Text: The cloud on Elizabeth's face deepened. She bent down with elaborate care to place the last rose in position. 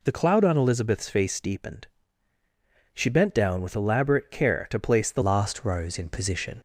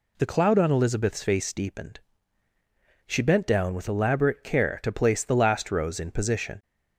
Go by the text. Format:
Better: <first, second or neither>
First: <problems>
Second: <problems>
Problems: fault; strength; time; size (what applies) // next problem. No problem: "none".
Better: second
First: changes voice at "last"; from 5.2 s on; 1.4 s long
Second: none